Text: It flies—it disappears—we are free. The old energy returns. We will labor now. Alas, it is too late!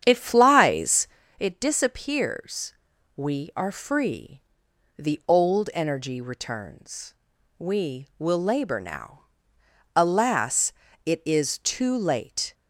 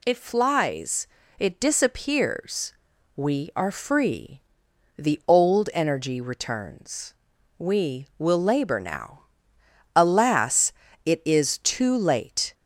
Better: second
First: starts louder than the rest; strong; until 1.2 s; 8.5 dB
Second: none

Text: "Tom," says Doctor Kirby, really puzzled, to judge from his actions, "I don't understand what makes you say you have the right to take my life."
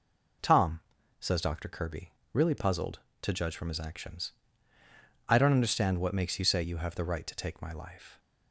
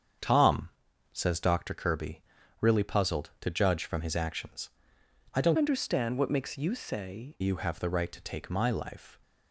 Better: first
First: none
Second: starts louder than the rest; strong; until 1.6 s; 7.5 dB // changes voice from "understand" to "say"; from 5.5 to 7.3 s; 1.8 s long

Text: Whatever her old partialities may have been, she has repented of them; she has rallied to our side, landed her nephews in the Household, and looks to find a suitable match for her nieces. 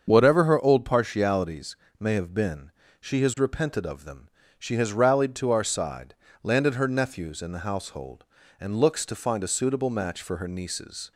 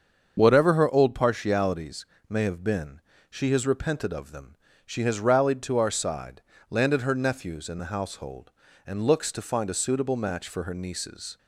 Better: neither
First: starts louder than the rest; until 1.1 s; 7 dB // pauses between "partialities" and "may"; slight; at 1.7 s; 0.22 s long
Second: starts louder than the rest; until 1.4 s; 7 dB // pauses between "partialities" and "may"; slight; at 2.0 s; 0.22 s long

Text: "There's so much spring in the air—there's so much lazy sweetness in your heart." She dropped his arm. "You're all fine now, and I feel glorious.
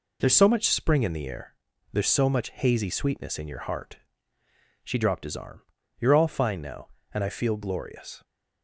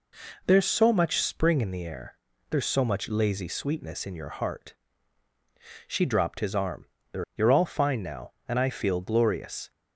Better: second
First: says "hazy" for "lazy"; at 2.5 s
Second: none

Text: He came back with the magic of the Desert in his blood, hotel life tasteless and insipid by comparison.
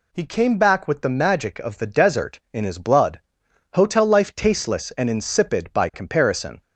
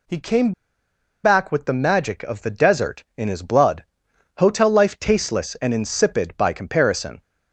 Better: first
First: none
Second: pauses between "came" and "back"; noticeable; at 0.5 s; 0.72 s long

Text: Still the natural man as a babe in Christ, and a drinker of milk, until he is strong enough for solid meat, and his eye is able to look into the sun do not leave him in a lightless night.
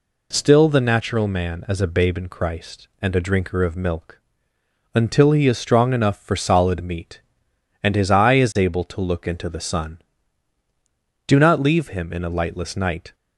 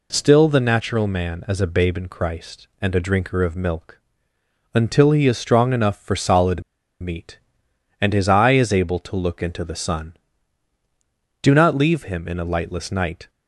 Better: first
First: none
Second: pauses between "solid" and "meat"; at 6.6 s; 0.39 s long

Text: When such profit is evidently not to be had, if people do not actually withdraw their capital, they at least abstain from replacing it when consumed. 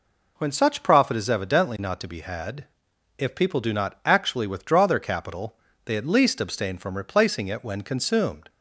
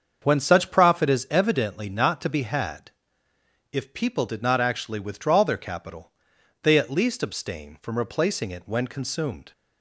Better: first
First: none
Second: starts louder than the rest; until 1.2 s; 7 dB // says "did" for "do"; at 4.2 s

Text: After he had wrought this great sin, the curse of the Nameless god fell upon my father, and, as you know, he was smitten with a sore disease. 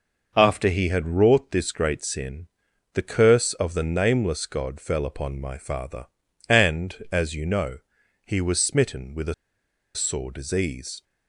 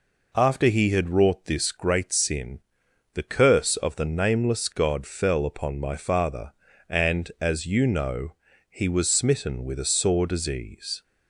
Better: second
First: pauses between "a" and "sore"; noticeable; at 9.3 s; 0.61 s long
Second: none

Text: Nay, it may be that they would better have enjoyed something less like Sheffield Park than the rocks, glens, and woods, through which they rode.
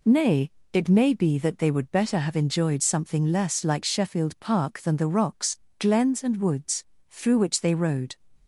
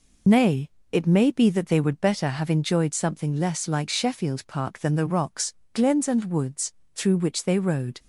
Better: first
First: none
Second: loses the start of "Nay"; at 0.2 s; 65 ms

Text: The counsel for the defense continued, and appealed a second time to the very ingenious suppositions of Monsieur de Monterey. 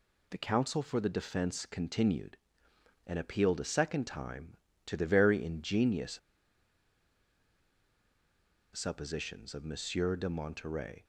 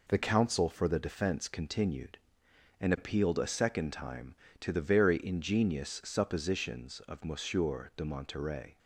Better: second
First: pauses between "ingenious" and "suppositions"; strong; at 6.1 s; 2.5 s long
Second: none

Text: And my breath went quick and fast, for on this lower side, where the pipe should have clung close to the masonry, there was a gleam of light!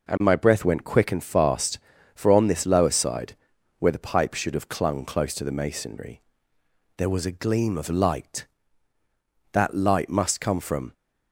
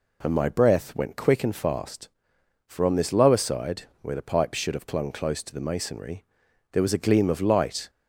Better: second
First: goes on to say "That light must come from"; from 9.5 s on; 1.4 s long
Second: none

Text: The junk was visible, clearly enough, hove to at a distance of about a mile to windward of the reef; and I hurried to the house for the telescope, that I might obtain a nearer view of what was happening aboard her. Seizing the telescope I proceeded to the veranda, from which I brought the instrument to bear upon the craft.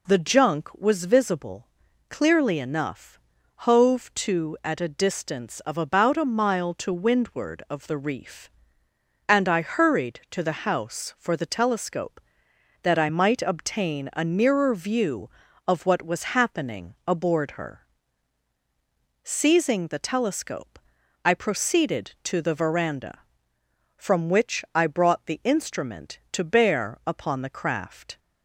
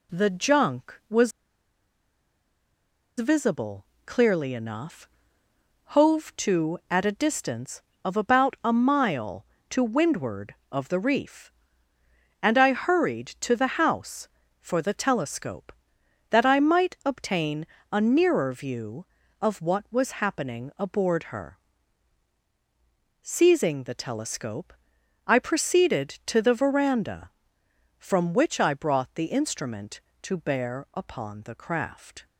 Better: first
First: pauses between "telescope" and "I"; at 20.8 s; 0.44 s long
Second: pauses between "was" and "visible"; strong; at 1.3 s; 1.8 s long // pauses between "obtain" and "a"; slight; at 17.6 s; 0.24 s long // pauses between "telescope" and "I"; noticeable; at 24.7 s; 0.52 s long

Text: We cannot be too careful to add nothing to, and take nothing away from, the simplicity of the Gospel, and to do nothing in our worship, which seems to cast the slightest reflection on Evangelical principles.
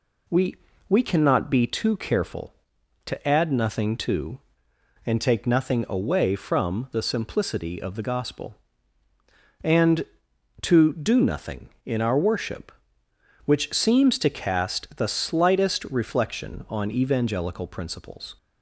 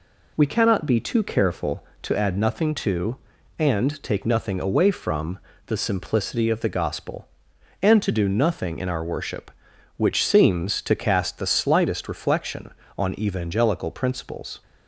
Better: second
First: says "We" twice; at 0.8 s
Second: none

